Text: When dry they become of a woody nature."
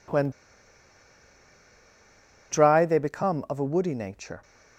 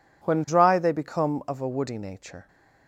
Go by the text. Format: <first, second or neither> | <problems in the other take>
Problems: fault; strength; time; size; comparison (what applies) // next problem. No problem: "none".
second | pauses between "When" and "dry"; strong; at 0.3 s; 2.2 s long